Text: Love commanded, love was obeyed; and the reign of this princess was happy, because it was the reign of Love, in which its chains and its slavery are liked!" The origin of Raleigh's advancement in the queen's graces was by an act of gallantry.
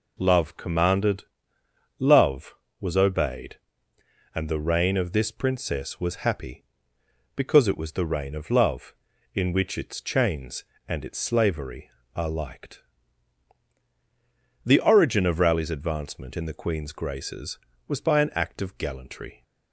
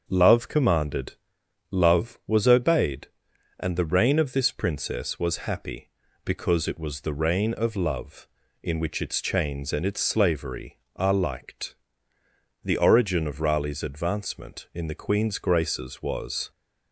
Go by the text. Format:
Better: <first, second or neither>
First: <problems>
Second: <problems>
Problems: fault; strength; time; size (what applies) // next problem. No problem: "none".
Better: first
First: none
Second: starts louder than the rest; until 1.0 s; 7 dB // stops before "by an act of gallantry"; at 16.5 s